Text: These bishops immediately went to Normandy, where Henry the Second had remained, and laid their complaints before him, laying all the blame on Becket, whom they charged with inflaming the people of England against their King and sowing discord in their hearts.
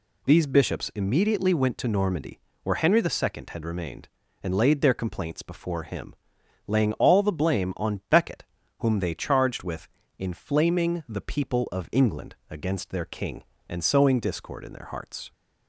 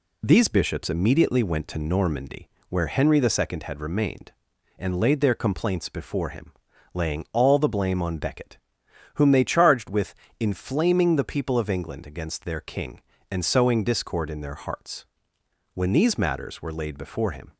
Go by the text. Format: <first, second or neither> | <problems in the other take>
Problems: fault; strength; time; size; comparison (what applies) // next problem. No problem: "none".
first | pauses between "with" and "inflaming"; slight; at 10.1 s; 0.24 s long; slight in the first // goes on to say "When these matters were laid before him"; strong; from 15.7 s on; 1.8 s long